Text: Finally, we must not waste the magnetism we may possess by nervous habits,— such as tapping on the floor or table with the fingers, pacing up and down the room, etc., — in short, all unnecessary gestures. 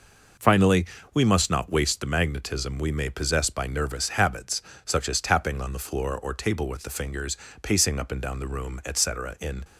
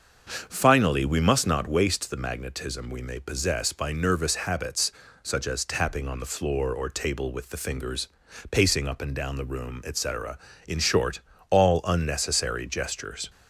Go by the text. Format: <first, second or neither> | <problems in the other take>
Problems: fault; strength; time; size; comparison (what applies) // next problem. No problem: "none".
second | stops before "short all unnecessary gestures"; at 9.6 s